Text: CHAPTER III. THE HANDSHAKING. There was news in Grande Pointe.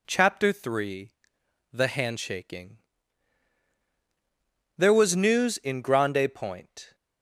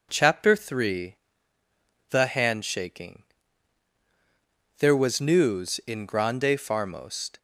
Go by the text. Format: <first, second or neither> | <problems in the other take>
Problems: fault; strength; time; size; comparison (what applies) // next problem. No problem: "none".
first | says "Farmost" for "Pointe"; at 6.5 s